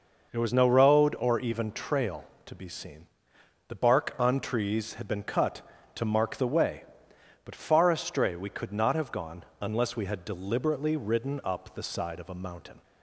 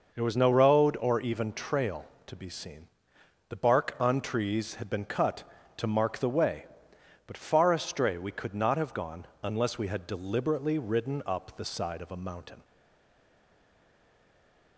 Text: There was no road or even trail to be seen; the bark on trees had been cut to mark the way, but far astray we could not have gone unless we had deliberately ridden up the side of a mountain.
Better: first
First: none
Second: stays silent after the last word; from 12.6 s on; 2.1 s long

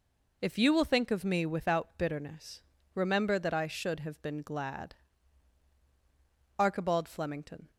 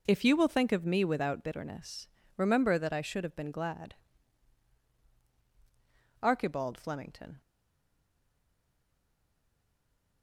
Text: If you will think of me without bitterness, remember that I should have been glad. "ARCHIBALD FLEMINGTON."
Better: first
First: none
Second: stays silent after the last word; strong; from 7.4 s on; 2.8 s long

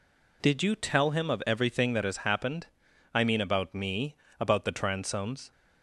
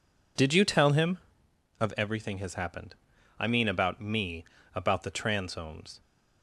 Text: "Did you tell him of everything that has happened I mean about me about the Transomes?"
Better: first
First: pauses between "happened" and "I"; at 2.6 s; 0.44 s long // pauses between "me" and "about"; slight; at 4.1 s; 0.24 s long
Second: skips "that"; at 2.3 s // pauses between "happened" and "I"; at 2.9 s; 0.44 s long // pauses between "me" and "about"; slight; at 4.4 s; 0.32 s long

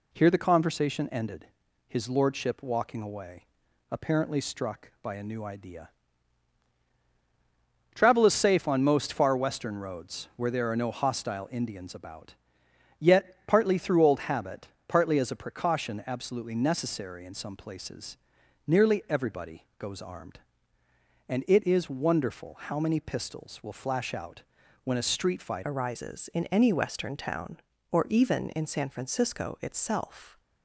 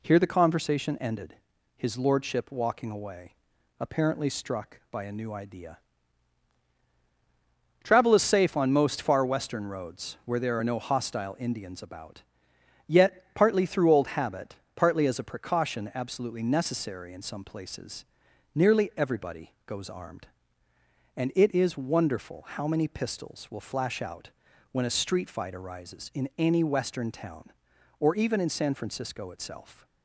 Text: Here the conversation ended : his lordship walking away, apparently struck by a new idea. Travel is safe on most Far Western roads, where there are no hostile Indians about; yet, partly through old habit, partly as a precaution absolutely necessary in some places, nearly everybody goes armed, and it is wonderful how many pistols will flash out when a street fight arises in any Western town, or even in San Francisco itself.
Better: second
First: pauses between "out" and "when"; at 24.4 s; 0.42 s long // changes voice at "arises"; from 25.6 s on; 4.7 s long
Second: pauses between "out" and "when"; at 24.2 s; 0.42 s long

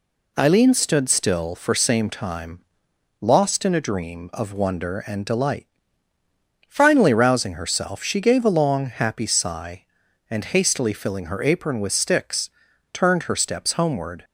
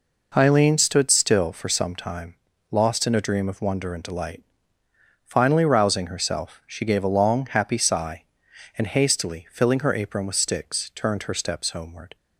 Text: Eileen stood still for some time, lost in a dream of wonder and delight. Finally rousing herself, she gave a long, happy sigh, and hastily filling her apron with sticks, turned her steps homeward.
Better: second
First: says "same" for "some"; at 1.7 s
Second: none

